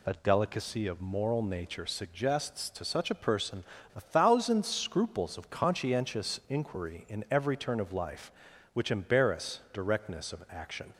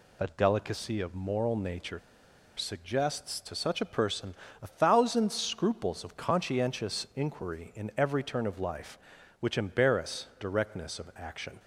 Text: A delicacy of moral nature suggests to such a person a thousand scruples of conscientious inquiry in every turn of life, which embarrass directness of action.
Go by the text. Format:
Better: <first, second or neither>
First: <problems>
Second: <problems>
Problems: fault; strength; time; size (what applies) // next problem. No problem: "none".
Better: first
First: pauses between "person" and "a"; slight; at 3.6 s; 0.30 s long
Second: pauses between "nature" and "suggests"; noticeable; at 1.9 s; 0.58 s long // pauses between "person" and "a"; slight; at 4.3 s; 0.26 s long